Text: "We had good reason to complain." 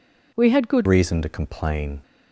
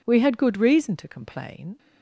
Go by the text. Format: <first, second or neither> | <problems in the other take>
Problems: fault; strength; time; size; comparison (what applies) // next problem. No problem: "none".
second | changes voice at "reason"; from 0.8 s on; 1.2 s long